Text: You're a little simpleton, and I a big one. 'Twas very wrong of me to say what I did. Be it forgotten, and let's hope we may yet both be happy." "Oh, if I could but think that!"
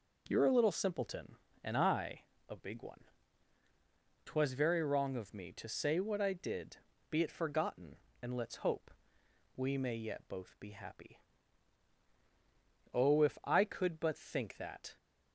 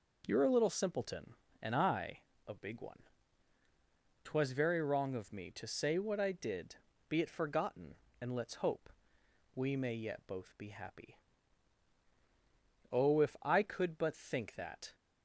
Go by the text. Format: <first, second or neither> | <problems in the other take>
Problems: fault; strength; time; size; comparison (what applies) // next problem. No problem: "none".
neither | pauses between "I" and "a"; slight; the same in both // pauses between "hope" and "we"; noticeable; the same in both